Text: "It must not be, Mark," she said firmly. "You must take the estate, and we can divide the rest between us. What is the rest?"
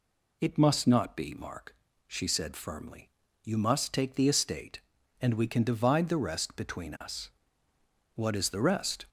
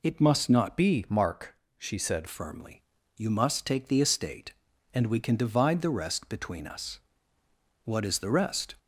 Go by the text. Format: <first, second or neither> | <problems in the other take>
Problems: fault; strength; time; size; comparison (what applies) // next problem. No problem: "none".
first | changes voice from "be" to "said"; from 0.7 to 2.2 s; 1.5 s long